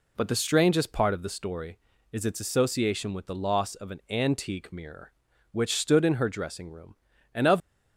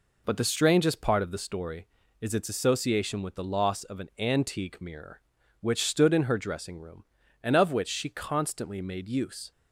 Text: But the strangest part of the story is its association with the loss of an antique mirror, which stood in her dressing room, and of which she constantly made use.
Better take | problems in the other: second | stops before "which she constantly made use"; at 7.6 s

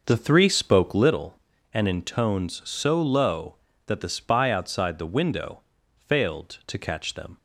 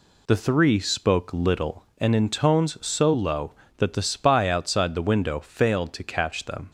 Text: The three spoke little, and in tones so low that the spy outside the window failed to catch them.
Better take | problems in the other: second | starts louder than the rest; noticeable; until 1.2 s; 6 dB // pauses between "window" and "failed"; slight; at 5.6 s; 0.34 s long

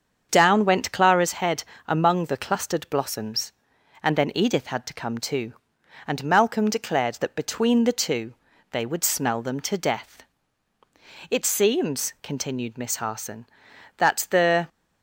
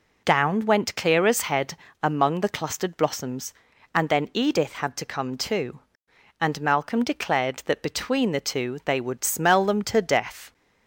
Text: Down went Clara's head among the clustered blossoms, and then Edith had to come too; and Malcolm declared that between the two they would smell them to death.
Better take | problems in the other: second | starts louder than the rest; until 1.3 s; 7 dB // pauses between "head" and "among"; slight; at 1.6 s; 0.24 s long; slight in the second // pauses between "two" and "they"; slight; at 8.3 s; 0.36 s long // goes on to say "It seems continued Miss Harson that the"; strong; from 11.3 s on; 3.3 s long

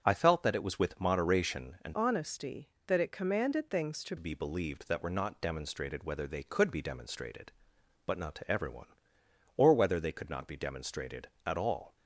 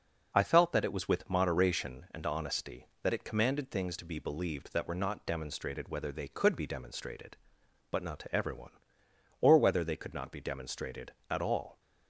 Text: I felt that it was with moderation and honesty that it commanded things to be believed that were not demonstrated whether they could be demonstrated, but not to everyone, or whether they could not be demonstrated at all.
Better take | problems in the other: second | starts louder than the rest; strong; until 1.0 s; 7.5 dB // changes voice from "honesty" to "to"; from 1.9 to 4.1 s; 2.2 s long

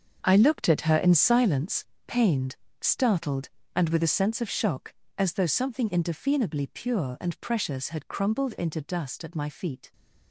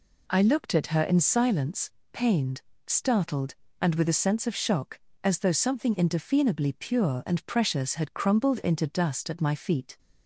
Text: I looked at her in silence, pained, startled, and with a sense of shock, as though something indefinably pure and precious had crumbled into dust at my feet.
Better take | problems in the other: second | gets quieter; strong; throughout; 13 dB

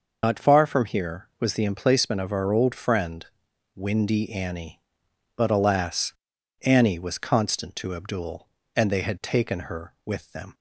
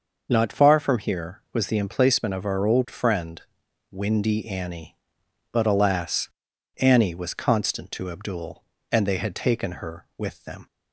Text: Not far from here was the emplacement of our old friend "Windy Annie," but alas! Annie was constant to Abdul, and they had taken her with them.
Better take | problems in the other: second | loses the start of "Not"; at 0.2 s; 70 ms // pauses between "friend" and "Windy"; noticeable; at 3.2 s; 0.52 s long; noticeable in the second

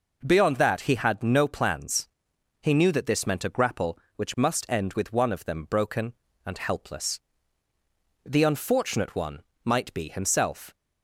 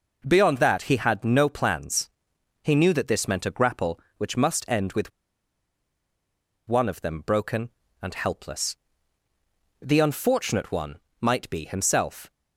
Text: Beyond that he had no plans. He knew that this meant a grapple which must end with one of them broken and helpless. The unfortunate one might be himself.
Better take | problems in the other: first | pauses between "with" and "one"; strong; at 5.1 s; 1.5 s long // pauses between "one" and "might"; slight; at 10.9 s; 0.24 s long; slight in the first

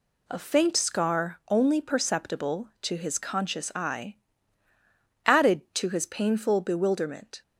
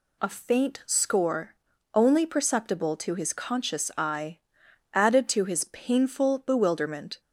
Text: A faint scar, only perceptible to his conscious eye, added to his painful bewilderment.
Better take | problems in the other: first | says "score" for "scar"; at 0.8 s

